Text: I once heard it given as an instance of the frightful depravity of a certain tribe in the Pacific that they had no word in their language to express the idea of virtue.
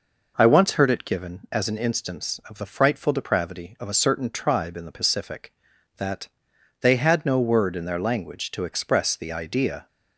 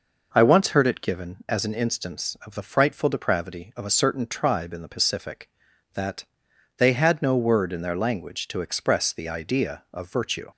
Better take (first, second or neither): second